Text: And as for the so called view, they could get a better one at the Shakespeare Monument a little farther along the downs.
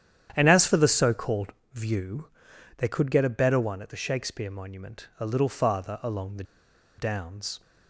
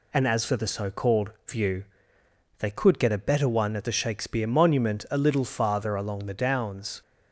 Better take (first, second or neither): second